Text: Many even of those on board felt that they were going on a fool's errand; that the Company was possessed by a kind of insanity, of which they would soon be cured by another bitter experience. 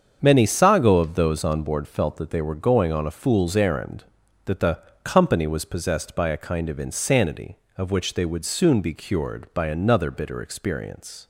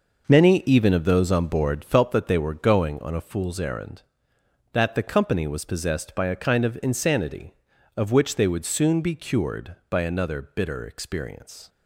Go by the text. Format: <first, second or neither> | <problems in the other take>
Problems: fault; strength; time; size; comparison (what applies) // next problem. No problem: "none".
second | starts louder than the rest; strong; until 1.2 s; 7 dB // says "sago" for "even"; at 0.4 s // pauses between "the" and "Company"; slight; at 4.7 s; 0.24 s long